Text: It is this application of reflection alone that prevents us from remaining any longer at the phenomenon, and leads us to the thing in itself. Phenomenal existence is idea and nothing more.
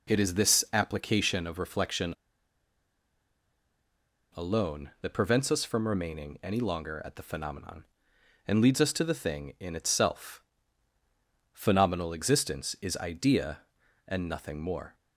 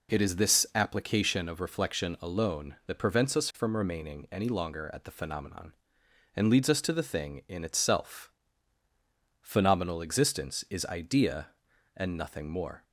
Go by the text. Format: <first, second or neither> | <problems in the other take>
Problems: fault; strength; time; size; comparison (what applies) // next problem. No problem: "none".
second | pauses between "reflection" and "alone"; strong; at 2.1 s; 2.2 s long